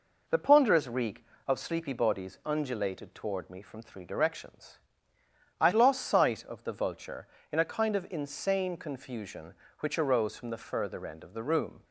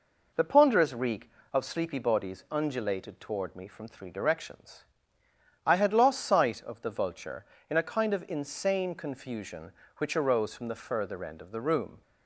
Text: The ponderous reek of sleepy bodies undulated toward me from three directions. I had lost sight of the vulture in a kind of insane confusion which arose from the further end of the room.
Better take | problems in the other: second | skips "had"; at 5.7 s

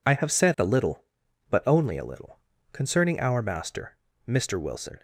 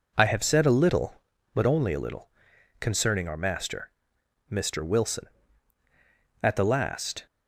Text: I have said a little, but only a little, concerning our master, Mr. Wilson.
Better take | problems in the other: first | goes on to say "At the last"; noticeable; from 6.4 s on; 0.84 s long

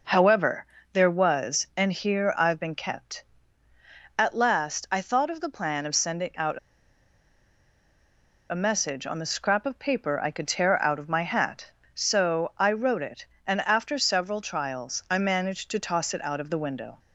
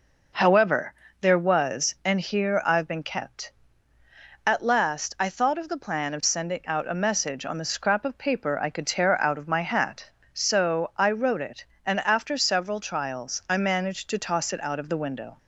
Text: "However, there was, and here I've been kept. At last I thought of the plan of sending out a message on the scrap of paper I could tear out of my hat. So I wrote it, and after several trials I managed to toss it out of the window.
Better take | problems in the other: second | pauses between "out" and "a"; strong; at 6.5 s; 1.9 s long

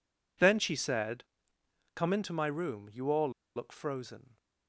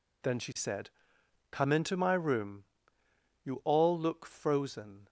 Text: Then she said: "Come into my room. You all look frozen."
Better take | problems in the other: second | pauses between "all" and "look"; slight; at 3.2 s; 0.26 s long

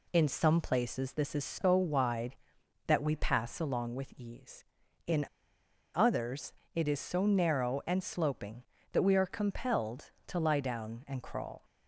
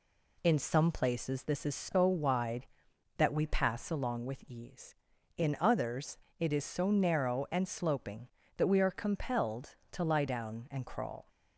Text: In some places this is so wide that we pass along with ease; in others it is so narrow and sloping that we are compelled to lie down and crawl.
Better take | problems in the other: second | pauses between "in" and "others"; noticeable; at 5.2 s; 0.67 s long // pauses between "others" and "it"; slight; at 6.5 s; 0.22 s long; slight in the second

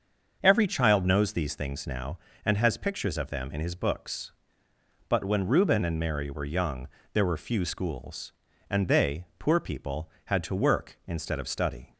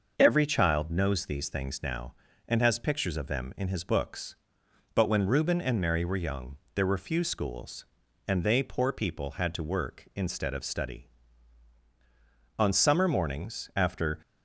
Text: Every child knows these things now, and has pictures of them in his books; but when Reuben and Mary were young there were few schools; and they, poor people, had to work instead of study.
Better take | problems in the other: first | starts louder than the rest; until 1.1 s; 6 dB; also in the first // pauses between "young" and "there"; slight; at 6.5 s; 0.18 s long; slight in the first // goes on to say "On summer mornings after"; from 12.5 s on; 1.6 s long

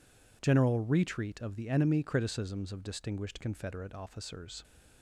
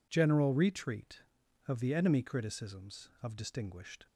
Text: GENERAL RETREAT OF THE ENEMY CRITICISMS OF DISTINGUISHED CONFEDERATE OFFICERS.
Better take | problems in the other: first | stops before "CONFEDERATE OFFICERS"; at 4.0 s

